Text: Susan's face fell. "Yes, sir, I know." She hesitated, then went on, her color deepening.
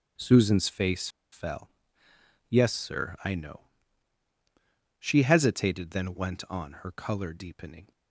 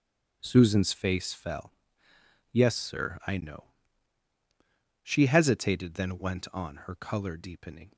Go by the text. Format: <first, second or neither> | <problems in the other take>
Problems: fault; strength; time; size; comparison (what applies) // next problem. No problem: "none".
second | starts louder than the rest; strong; until 1.4 s; 8 dB; strong in the second // pauses between "face" and "fell"; slight; at 1.0 s; 0.24 s long